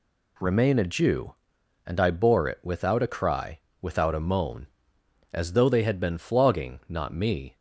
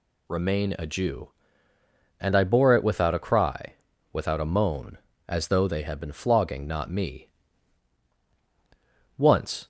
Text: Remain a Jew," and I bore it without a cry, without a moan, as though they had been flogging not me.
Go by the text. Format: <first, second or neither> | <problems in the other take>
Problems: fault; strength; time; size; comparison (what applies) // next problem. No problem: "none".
first | goes on to say "Once"; from 9.1 s on; 0.50 s long